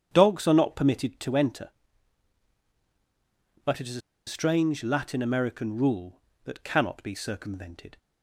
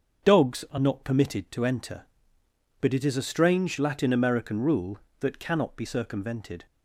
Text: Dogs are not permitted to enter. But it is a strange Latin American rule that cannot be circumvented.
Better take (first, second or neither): second